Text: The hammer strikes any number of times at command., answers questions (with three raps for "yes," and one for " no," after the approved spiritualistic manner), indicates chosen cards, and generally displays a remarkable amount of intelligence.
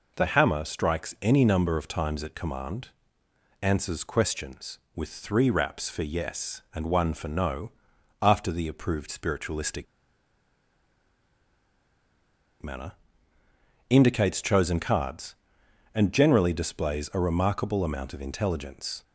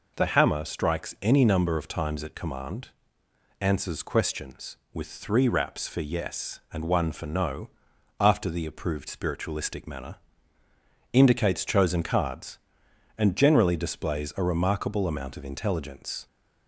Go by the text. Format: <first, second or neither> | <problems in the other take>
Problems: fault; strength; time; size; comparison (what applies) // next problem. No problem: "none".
second | pauses between "spiritualistic" and "manner"; strong; at 9.8 s; 2.7 s long